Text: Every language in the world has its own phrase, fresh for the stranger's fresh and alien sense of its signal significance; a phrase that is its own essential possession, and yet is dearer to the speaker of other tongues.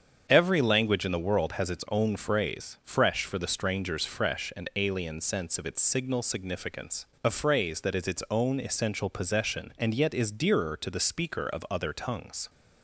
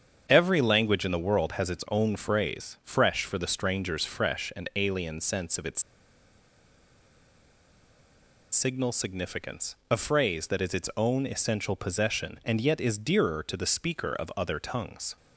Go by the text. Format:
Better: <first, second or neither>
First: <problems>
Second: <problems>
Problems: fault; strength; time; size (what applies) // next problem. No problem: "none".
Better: first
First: starts louder than the rest; strong; until 1.3 s; 7.5 dB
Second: starts louder than the rest; strong; until 1.3 s; 7.5 dB // pauses between "its" and "signal"; strong; at 5.8 s; 2.7 s long